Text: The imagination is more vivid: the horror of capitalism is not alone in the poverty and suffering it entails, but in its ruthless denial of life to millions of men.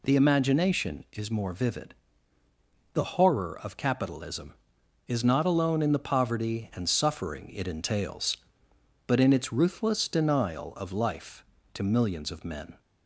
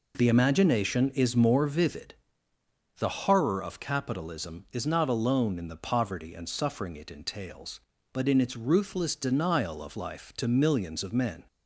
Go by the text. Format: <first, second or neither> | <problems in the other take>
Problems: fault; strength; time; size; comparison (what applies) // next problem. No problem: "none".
neither | none